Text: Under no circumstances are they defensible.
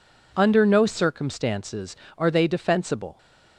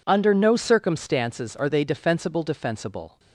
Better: first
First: none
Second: says "defensible" twice; at 2.4 s

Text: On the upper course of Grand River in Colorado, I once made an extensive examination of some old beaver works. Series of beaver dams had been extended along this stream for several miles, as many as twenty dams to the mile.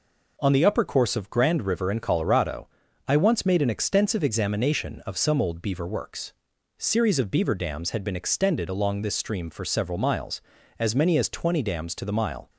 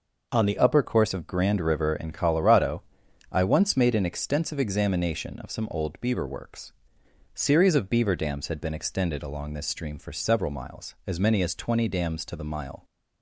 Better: first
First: none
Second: changes voice at "upper"; from 0.5 s on; 12.3 s long

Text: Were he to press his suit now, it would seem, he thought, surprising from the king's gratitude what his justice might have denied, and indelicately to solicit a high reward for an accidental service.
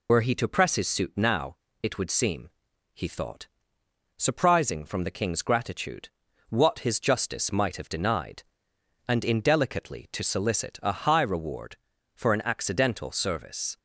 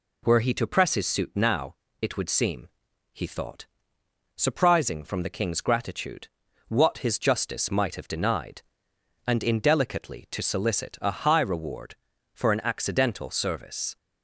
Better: second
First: loses the start of "Were"; at 0.0 s; 60 ms // pauses between "gratitude" and "what"; at 6.0 s; 0.40 s long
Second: pauses between "gratitude" and "what"; at 6.2 s; 0.40 s long

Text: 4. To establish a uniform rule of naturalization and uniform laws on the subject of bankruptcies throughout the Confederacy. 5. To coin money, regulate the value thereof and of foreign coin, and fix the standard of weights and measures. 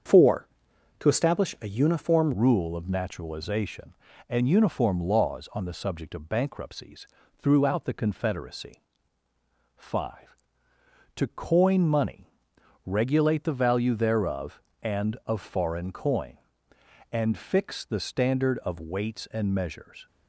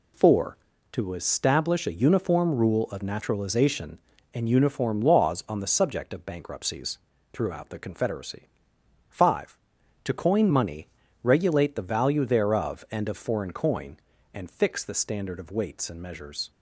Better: second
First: starts louder than the rest; strong; until 1.7 s; 7 dB // changes voice at "rule"; from 2.3 s on; 17.7 s long // pauses between "bankruptcies" and "throughout"; slight; at 7.0 s; 0.34 s long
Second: pauses between "bankruptcies" and "throughout"; slight; at 6.9 s; 0.34 s long

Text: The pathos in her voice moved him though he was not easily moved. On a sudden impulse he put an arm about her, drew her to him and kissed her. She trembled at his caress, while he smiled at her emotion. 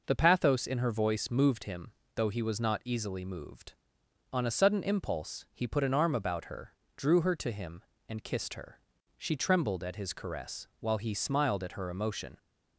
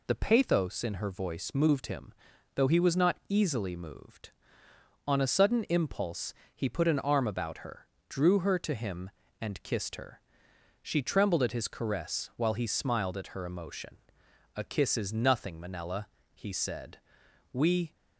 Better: first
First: pauses between "him" and "though"; slight; at 1.9 s; 0.24 s long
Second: pauses between "him" and "though"; at 2.1 s; 0.40 s long // pauses between "impulse" and "he"; slight; at 6.3 s; 0.20 s long // goes on to say "A kiss is nothing Manella he said We"; strong; from 14.5 s on; 3.4 s long

